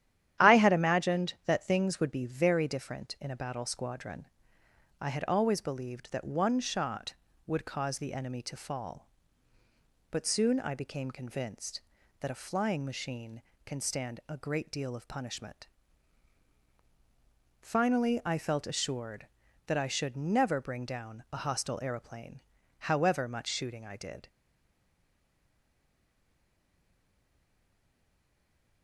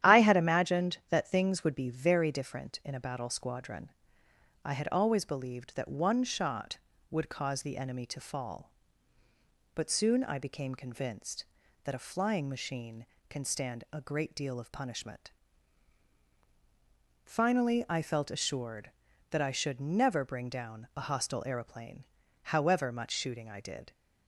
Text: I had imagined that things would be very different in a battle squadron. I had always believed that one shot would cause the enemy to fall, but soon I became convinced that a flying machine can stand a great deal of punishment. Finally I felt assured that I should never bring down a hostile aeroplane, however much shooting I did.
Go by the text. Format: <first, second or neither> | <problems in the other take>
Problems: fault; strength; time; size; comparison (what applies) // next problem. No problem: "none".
second | starts louder than the rest; strong; until 1.5 s; 11 dB; strong in the second // stays silent after the last word; strong; from 24.2 s on; 4.6 s long